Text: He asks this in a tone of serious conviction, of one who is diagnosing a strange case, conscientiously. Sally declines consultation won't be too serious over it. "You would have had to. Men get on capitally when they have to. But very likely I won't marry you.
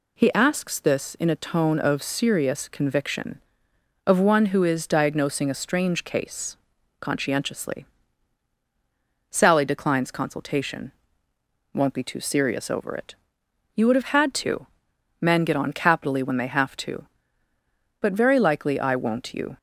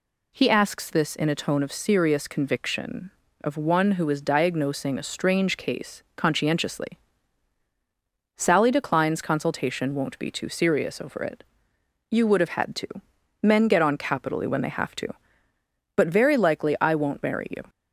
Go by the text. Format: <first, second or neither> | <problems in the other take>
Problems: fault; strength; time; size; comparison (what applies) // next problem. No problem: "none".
second | pauses between "consultation" and "won't"; noticeable; at 10.9 s; 0.84 s long // skips "marry"; at 19.3 s